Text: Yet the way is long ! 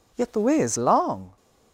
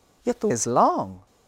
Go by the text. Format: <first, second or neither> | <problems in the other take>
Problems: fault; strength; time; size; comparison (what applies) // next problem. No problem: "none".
first | skips "way"; at 0.4 s